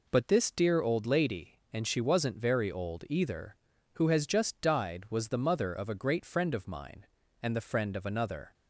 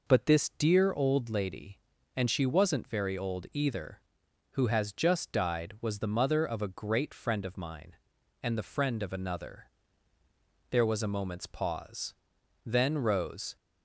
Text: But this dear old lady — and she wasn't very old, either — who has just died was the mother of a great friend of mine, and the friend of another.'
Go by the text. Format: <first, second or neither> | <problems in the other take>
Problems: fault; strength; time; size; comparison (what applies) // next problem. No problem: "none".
first | goes on to say "There was a moment's pause Then Rose"; strong; from 10.6 s on; 2.8 s long